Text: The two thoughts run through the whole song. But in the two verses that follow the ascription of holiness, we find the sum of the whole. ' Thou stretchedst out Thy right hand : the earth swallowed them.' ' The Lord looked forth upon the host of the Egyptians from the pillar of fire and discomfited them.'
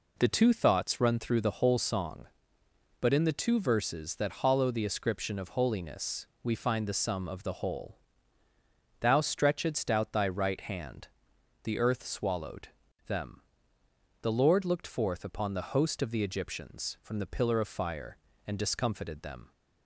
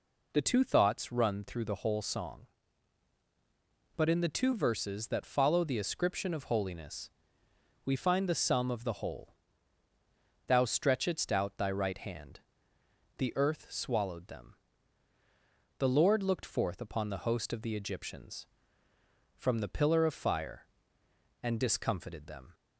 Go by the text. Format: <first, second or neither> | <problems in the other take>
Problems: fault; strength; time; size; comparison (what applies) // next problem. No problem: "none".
second | says "hollow" for "follow"; at 4.4 s // pauses between "swallowed" and "them"; slight; at 12.6 s; 0.36 s long